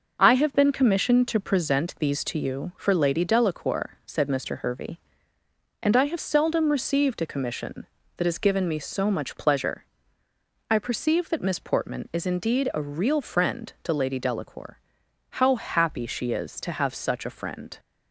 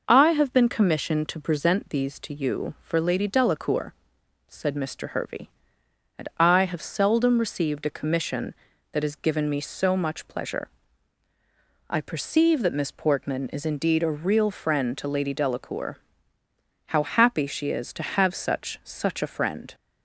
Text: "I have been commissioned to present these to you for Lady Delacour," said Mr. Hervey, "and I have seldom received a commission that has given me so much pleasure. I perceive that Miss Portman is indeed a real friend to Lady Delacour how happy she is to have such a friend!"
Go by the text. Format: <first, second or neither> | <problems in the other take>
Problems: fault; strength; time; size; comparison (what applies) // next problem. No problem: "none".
first | pauses between "Delacour" and "how"; noticeable; at 15.9 s; 0.92 s long; noticeable in the first // says "such" twice; at 18.8 s